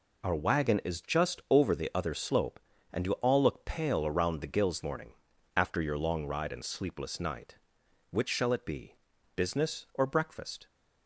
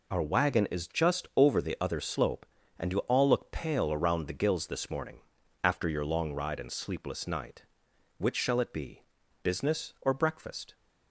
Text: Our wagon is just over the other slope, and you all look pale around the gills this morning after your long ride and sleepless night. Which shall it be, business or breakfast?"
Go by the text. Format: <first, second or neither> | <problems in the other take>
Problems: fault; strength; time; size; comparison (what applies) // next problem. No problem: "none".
second | skips "this"; at 4.8 s // pauses between "morning" and "after"; at 5.1 s; 0.42 s long; also in the second